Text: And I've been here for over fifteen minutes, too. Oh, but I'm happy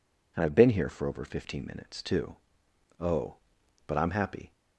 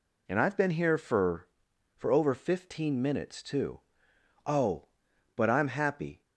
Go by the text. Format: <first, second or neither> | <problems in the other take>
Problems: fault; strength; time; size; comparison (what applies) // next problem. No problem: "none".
first | says "for" twice; at 1.9 s